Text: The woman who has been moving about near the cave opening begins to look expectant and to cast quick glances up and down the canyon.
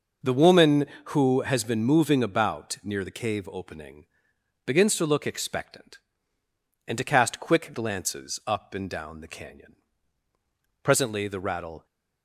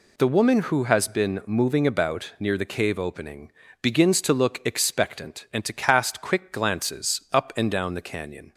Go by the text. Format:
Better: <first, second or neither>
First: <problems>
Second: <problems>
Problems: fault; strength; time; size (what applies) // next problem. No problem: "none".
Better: second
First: pauses between "opening" and "begins"; noticeable; at 4.0 s; 0.60 s long // goes on to say "Presently the rattle"; noticeable; from 10.8 s on; 1.0 s long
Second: pauses between "opening" and "begins"; slight; at 3.4 s; 0.32 s long